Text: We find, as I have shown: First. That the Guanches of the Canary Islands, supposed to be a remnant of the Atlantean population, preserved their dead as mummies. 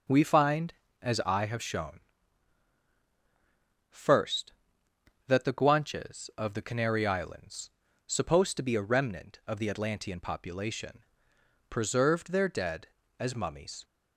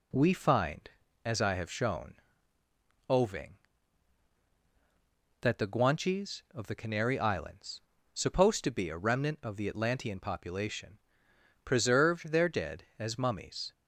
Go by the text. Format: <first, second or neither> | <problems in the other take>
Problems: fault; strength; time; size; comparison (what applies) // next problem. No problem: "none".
first | says "Oving" for "First"; at 3.0 s